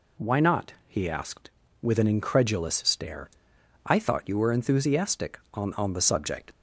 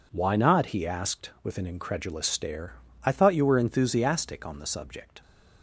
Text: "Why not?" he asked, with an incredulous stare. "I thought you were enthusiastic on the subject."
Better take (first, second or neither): second